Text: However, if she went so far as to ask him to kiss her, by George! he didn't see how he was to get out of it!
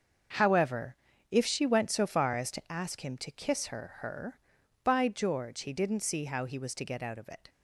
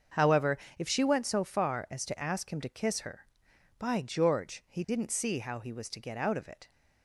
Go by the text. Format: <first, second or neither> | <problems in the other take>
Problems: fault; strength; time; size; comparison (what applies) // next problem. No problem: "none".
second | starts louder than the rest; until 1.7 s; 6.5 dB; also in the second // says "her" twice; at 3.9 s